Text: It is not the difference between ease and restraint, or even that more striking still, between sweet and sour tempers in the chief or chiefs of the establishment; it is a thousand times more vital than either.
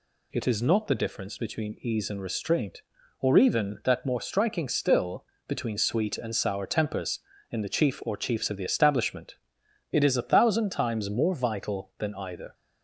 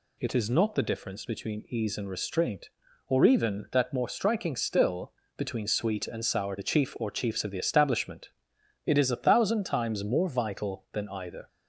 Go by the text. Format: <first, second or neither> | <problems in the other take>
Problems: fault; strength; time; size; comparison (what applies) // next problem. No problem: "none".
first | skips "tempers in"; at 6.5 s